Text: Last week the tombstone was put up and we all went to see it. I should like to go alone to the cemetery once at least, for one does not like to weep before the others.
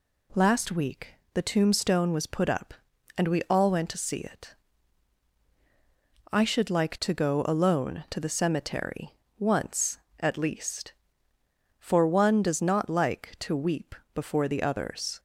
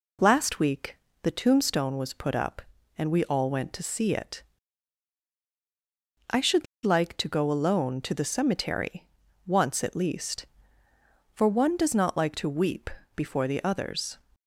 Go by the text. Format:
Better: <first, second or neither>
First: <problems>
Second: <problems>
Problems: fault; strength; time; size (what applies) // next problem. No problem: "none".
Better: first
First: pauses between "week" and "the"; slight; at 1.1 s; 0.18 s long // pauses between "cemetery" and "once"; slight; at 9.1 s; 0.24 s long // pauses between "weep" and "before"; slight; at 13.9 s; 0.22 s long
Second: pauses between "week" and "the"; slight; at 0.9 s; 0.24 s long // pauses between "should" and "like"; slight; at 6.6 s; 0.19 s long // pauses between "cemetery" and "once"; at 9.0 s; 0.44 s long // pauses between "weep" and "before"; slight; at 12.9 s; 0.24 s long